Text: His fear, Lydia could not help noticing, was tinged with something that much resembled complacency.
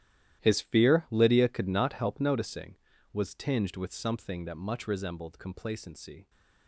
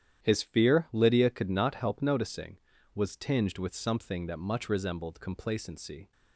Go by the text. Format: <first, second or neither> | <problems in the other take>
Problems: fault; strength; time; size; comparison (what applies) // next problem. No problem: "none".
second | gets quieter; strong; throughout; 15 dB // starts louder than the rest; strong; until 1.4 s; 12.5 dB; strong in the second